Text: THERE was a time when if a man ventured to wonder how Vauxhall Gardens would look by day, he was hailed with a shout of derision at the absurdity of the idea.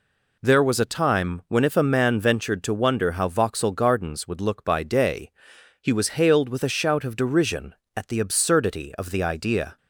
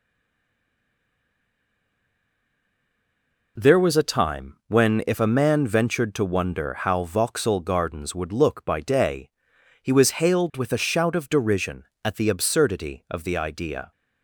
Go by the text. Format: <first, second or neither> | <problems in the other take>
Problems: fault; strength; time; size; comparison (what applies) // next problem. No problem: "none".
first | stays silent before the first word; strong; until 3.5 s; 3.5 s long